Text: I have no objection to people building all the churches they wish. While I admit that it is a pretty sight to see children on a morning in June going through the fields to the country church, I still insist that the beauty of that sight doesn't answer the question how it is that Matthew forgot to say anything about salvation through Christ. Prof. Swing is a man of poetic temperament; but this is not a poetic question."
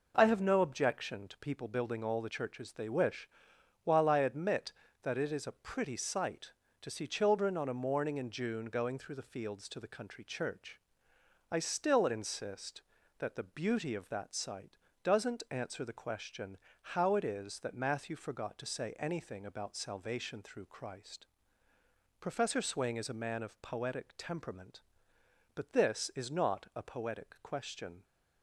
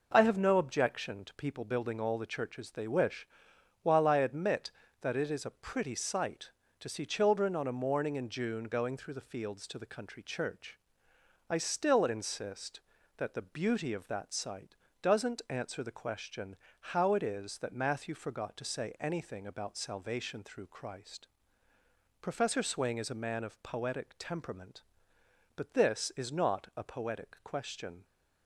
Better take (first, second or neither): neither